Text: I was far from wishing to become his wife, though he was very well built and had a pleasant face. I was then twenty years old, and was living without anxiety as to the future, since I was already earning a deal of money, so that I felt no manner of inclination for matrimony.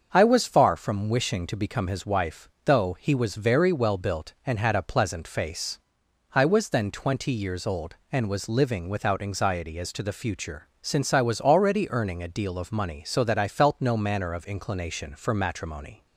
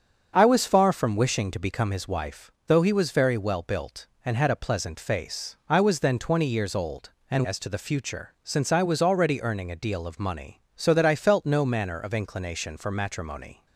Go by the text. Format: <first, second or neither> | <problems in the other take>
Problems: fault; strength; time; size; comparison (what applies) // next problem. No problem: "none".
first | starts louder than the rest; until 1.3 s; 7 dB; also in the first // skips "was living without anxiety"; at 7.4 s